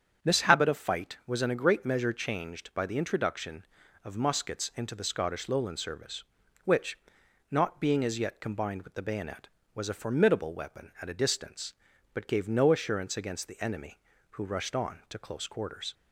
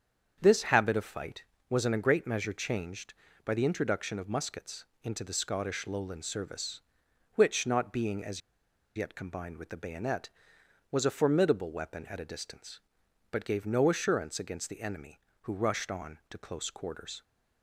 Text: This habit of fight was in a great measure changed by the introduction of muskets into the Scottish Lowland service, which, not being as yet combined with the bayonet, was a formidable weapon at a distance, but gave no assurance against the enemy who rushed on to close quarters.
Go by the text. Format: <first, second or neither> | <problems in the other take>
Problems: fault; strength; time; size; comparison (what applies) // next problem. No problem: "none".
first | starts louder than the rest; strong; until 1.4 s; 7.5 dB; strong in the first // pauses between "muskets" and "into"; slight; at 4.8 s; 0.18 s long // pauses between "as" and "yet"; noticeable; at 8.3 s; 0.55 s long